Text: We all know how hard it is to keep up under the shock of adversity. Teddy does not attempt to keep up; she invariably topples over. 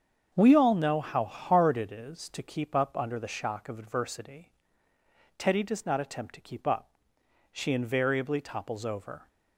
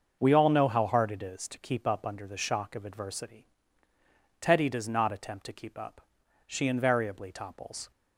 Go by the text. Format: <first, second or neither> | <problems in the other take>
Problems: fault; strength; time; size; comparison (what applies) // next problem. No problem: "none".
first | starts louder than the rest; until 1.2 s; 6.5 dB; strong in the first // stops before "over"; at 7.9 s